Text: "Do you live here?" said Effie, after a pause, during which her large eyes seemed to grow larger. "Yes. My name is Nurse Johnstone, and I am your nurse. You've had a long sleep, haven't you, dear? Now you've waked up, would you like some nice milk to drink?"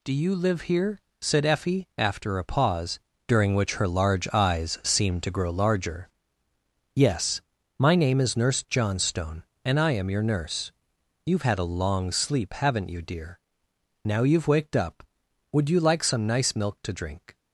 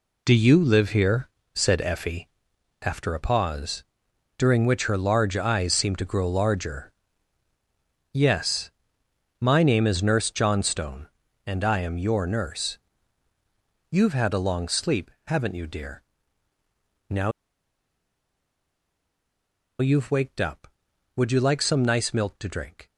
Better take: first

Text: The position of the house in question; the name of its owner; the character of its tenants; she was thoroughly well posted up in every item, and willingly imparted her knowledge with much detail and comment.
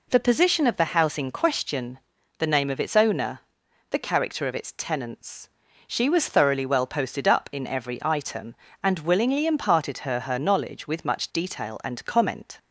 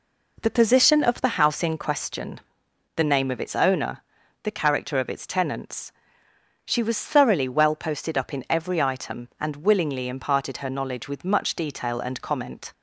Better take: second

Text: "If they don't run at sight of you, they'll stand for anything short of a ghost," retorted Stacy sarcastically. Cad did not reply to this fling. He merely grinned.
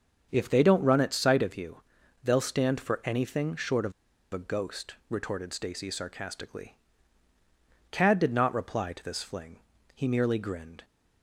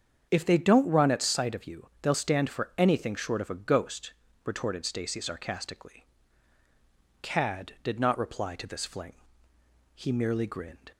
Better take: second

